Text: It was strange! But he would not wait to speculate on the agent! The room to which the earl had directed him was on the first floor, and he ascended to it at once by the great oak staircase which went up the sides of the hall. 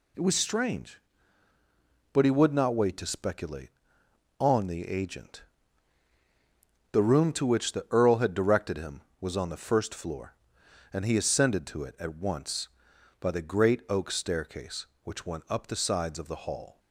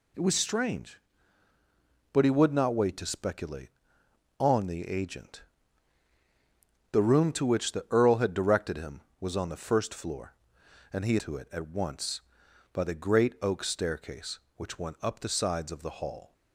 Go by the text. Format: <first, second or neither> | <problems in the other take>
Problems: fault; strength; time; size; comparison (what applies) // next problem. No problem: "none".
first | skips "ascended"; at 11.1 s